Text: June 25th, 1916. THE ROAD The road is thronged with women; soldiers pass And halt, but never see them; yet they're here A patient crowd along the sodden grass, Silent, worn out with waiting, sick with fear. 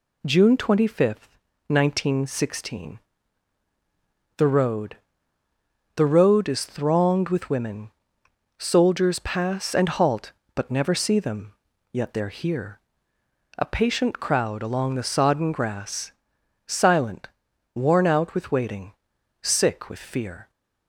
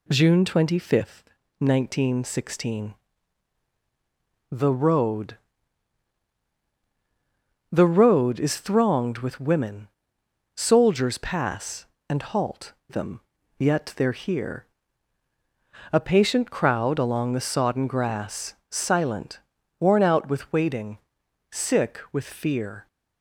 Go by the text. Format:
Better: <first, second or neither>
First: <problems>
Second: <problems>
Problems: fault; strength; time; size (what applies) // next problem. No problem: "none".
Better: first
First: pauses between "ROAD" and "The"; noticeable; at 4.9 s; 0.98 s long // pauses between "here" and "A"; noticeable; at 12.7 s; 0.78 s long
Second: pauses between "ROAD" and "The"; strong; at 5.3 s; 2.3 s long // skips "but never see"; at 12.8 s // pauses between "here" and "A"; strong; at 14.6 s; 1.2 s long